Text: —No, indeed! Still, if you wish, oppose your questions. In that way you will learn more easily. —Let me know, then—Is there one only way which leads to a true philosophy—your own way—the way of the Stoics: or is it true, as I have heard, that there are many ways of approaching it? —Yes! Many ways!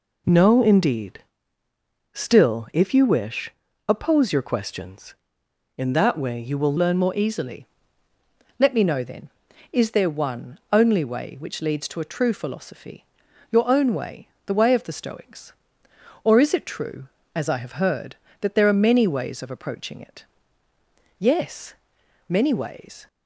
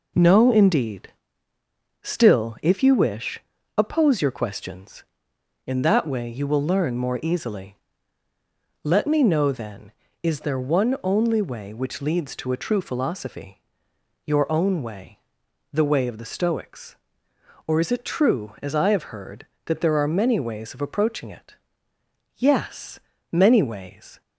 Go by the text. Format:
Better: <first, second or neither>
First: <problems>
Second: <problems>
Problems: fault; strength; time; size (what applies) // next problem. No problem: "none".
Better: second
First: changes voice at "learn"; from 6.7 s on; 16.3 s long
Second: none